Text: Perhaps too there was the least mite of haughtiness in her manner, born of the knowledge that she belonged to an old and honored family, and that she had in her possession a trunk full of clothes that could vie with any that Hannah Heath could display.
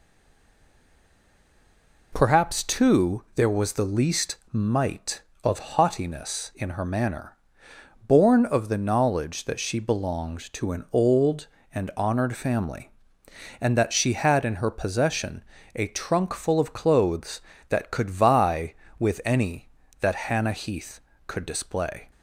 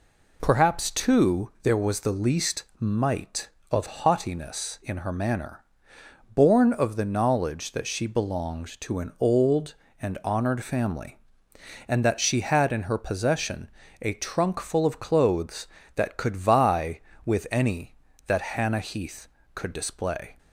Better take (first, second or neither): second